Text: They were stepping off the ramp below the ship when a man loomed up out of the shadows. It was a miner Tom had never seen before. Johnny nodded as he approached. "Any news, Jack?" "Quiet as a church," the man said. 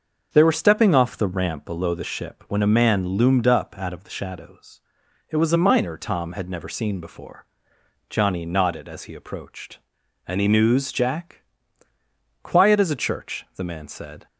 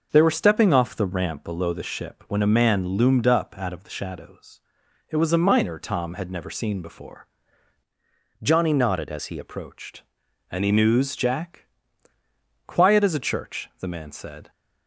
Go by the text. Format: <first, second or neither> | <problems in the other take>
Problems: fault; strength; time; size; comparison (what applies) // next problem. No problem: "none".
first | starts louder than the rest; noticeable; until 1.1 s; 6 dB; also in the first // changes voice from "Johnny" to "he"; from 8.4 to 9.3 s; 0.9 s long